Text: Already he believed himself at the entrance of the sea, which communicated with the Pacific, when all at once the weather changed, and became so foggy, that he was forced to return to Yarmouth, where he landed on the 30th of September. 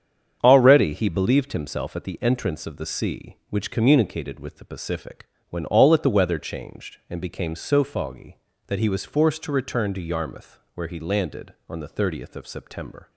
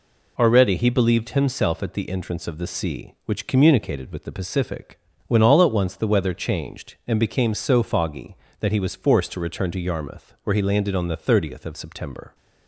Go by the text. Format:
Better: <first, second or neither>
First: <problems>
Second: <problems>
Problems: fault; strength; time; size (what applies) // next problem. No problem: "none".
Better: second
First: starts louder than the rest; strong; until 1.4 s; 8 dB // skips "once"; at 6.0 s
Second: none